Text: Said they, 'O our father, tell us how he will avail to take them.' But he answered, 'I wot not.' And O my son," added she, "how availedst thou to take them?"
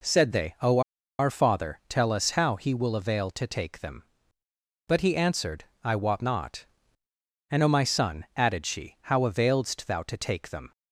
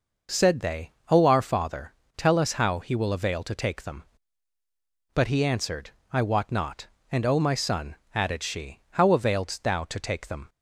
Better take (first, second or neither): second